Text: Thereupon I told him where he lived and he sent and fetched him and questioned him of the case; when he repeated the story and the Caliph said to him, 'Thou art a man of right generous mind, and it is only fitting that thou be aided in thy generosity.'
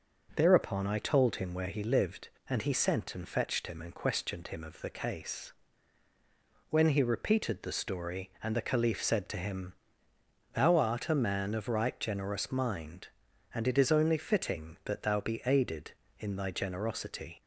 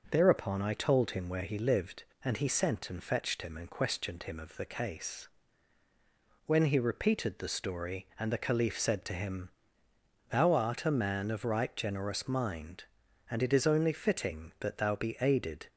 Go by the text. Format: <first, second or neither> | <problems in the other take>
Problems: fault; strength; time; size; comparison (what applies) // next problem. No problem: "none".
first | stops before "in thy generosity"; at 15.6 s